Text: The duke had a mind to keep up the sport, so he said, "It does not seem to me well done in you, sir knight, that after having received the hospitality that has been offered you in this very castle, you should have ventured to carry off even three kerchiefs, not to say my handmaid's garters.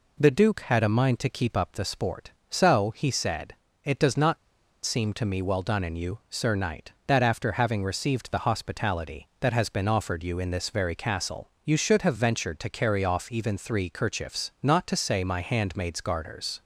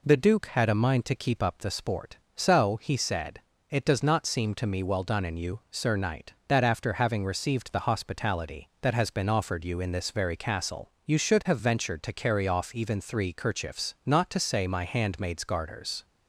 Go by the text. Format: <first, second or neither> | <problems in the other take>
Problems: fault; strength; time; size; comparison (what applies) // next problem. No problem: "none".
second | pauses between "not" and "seem"; noticeable; at 4.3 s; 0.47 s long